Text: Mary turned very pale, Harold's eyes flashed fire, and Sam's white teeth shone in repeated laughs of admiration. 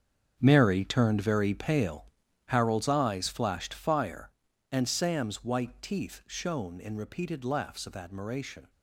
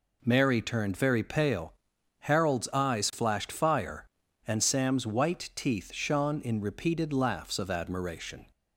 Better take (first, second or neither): second